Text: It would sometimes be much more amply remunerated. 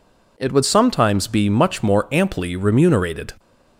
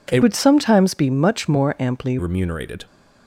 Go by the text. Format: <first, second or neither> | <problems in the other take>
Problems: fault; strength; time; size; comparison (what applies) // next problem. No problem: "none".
first | changes voice from "would" to "amply"; from 0.2 to 2.1 s; 1.9 s long